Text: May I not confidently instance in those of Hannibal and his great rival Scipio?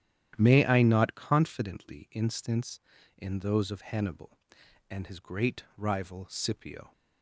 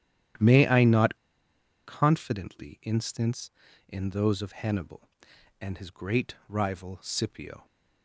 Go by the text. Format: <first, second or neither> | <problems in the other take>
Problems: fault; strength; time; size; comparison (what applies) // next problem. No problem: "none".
first | starts louder than the rest; strong; until 2.0 s; 11 dB; strong in the first // pauses between "not" and "confidently"; noticeable; at 1.1 s; 0.70 s long